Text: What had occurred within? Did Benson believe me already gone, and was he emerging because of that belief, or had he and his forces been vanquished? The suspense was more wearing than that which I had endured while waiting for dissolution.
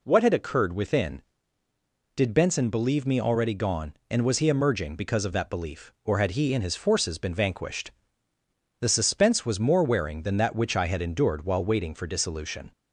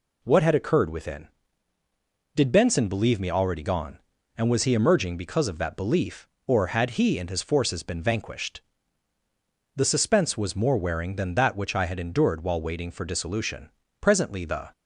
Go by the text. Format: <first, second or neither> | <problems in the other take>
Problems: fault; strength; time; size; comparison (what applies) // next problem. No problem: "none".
first | goes on to say "Presently the"; noticeable; from 13.9 s on; 0.72 s long